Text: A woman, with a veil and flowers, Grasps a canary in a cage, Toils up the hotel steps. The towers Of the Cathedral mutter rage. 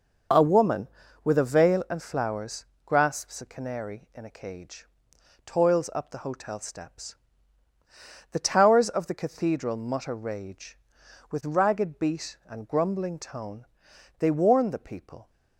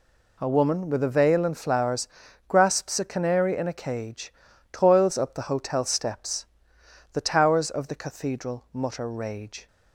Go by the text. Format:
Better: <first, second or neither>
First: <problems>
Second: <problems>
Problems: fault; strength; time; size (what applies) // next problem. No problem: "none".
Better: second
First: goes on to say "With ragged beat and grumbling tone They warn the people"; strong; from 11.3 s on; 3.9 s long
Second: none